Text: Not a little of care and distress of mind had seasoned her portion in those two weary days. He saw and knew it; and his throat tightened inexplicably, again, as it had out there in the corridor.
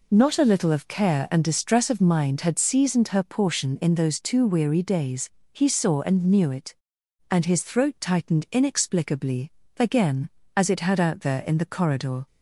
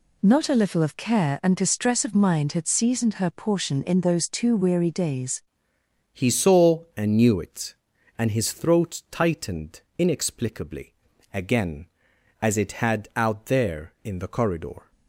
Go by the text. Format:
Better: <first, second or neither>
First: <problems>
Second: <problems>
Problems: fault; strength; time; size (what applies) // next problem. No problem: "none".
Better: first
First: none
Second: changes voice at "He"; from 6.1 s on; 8.8 s long